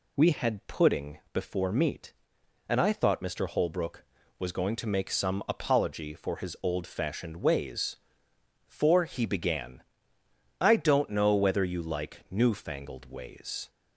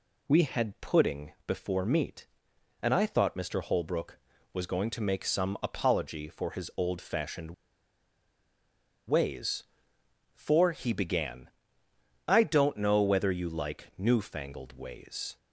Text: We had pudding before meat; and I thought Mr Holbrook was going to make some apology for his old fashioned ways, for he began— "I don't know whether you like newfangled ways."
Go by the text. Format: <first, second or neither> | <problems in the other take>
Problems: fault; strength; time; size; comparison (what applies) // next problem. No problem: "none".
first | pauses between "fashioned" and "ways"; strong; at 7.5 s; 1.5 s long